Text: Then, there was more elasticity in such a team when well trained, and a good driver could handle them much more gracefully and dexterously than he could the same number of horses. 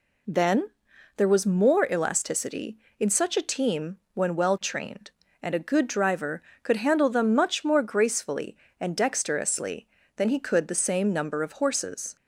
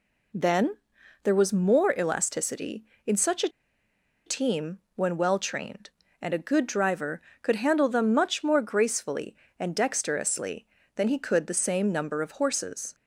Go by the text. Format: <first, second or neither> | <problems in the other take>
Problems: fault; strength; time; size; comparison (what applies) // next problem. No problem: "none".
first | pauses between "a" and "team"; noticeable; at 3.4 s; 0.76 s long // pauses between "team" and "when"; slight; at 4.7 s; 0.16 s long; slight in the first